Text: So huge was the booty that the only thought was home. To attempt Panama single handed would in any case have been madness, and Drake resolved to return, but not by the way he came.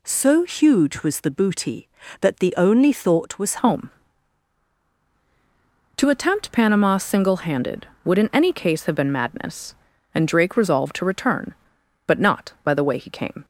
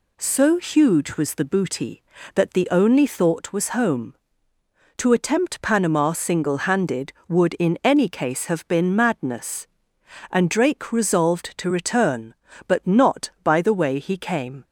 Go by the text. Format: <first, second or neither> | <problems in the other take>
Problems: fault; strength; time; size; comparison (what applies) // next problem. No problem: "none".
second | changes voice at "home"; from 3.5 s on; 9.9 s long